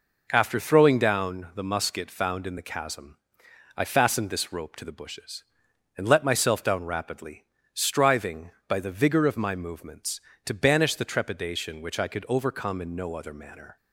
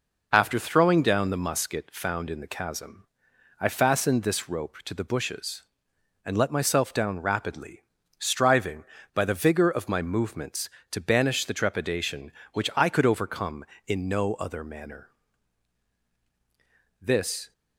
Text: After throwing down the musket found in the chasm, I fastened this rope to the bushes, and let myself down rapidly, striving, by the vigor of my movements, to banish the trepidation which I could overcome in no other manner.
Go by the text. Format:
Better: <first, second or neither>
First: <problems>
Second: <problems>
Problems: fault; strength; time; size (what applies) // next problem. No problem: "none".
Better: first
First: none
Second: goes on to say "This"; from 16.9 s on; 0.52 s long